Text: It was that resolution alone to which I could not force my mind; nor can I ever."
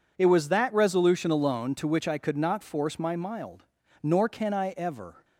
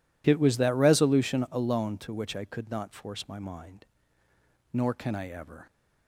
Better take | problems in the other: second | says "mild" for "mind"; at 3.1 s

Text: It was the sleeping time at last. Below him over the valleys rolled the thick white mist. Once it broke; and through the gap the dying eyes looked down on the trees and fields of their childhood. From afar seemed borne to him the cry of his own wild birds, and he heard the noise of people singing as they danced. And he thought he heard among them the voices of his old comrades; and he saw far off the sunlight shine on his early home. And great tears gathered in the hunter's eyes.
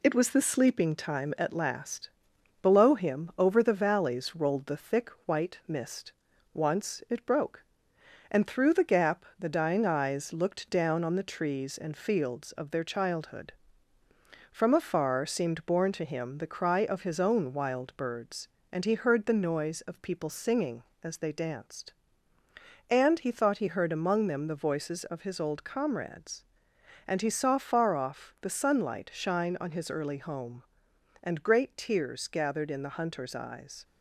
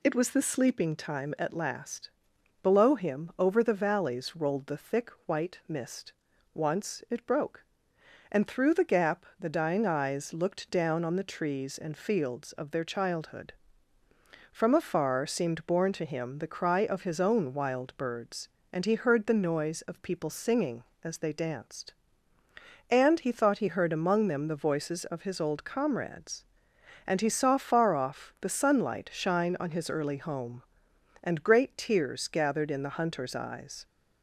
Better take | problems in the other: second | gets quieter; throughout; 3.5 dB // pauses between "thick" and "white"; slight; at 5.1 s; 0.16 s long; slight in the second

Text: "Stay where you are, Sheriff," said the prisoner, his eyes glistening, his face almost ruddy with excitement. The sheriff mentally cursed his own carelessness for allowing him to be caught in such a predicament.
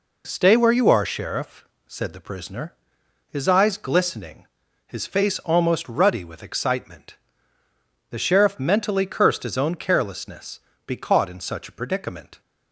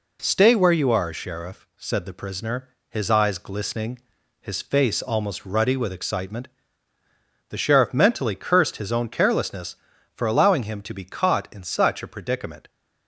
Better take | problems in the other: second | skips "for allowing him to"; at 10.7 s

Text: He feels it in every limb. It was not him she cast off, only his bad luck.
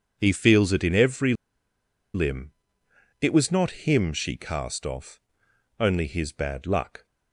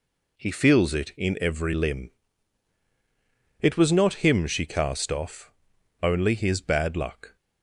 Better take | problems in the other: second | pauses between "every" and "limb"; noticeable; at 1.3 s; 0.81 s long

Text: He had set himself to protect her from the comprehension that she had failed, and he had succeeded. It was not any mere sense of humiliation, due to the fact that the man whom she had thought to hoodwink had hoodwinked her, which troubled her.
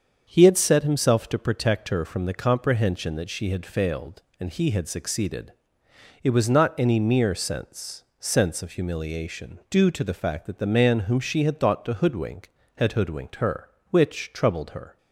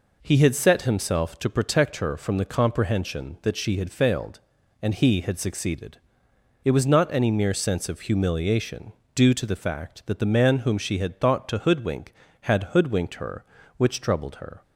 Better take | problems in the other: second | starts louder than the rest; until 1.2 s; 7 dB // says "sense" twice; at 8.1 s

